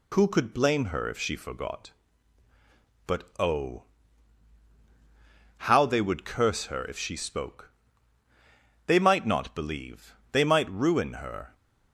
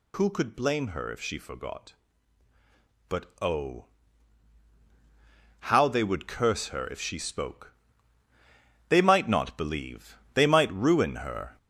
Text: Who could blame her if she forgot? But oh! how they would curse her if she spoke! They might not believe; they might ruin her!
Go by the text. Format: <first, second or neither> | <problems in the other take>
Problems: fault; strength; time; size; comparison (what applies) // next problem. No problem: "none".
first | gets louder; throughout; 3.5 dB // pauses between "But" and "oh"; slight; at 3.2 s; 0.16 s long; slight in the first